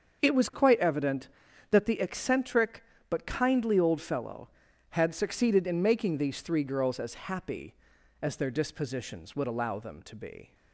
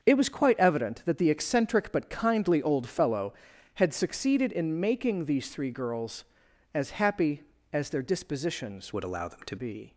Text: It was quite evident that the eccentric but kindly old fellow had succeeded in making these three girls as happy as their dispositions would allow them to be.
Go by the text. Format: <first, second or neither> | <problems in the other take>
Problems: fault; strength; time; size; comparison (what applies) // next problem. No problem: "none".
first | starts louder than the rest; until 1.0 s; 7 dB; also in the first // changes voice from "would" to "to"; from 8.9 to 9.5 s; 0.6 s long